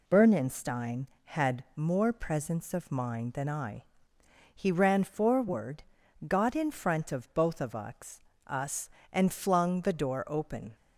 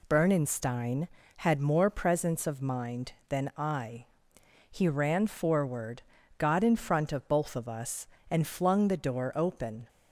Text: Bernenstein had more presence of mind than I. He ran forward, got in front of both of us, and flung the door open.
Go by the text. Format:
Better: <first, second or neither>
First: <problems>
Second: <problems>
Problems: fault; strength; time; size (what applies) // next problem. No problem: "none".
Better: second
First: says "us" twice; at 8.4 s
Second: none